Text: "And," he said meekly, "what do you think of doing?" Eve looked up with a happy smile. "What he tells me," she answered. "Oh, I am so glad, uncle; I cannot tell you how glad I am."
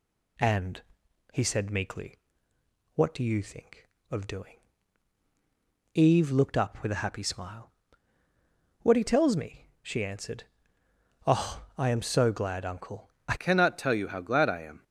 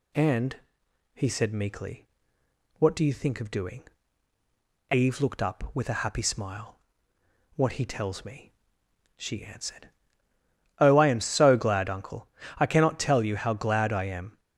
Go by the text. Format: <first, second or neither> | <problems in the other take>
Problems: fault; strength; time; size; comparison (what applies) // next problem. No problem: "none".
second | changes voice at "cannot"; from 13.3 s on; 1.5 s long